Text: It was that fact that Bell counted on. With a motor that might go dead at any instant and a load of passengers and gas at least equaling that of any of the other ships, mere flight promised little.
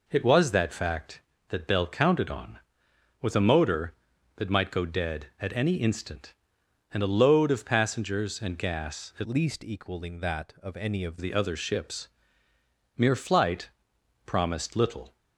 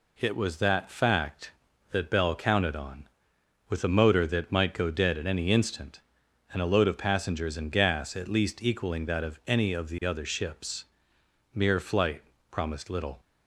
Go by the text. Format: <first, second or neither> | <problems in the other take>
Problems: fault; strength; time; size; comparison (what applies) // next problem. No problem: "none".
second | changes voice from "least" to "of"; from 9.2 to 11.1 s; 1.9 s long // pauses between "flight" and "promised"; noticeable; at 13.6 s; 0.56 s long; slight in the second